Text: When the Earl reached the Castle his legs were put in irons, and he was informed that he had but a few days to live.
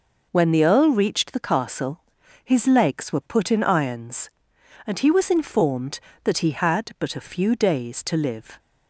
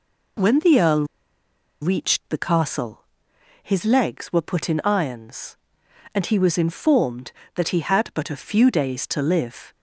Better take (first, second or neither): first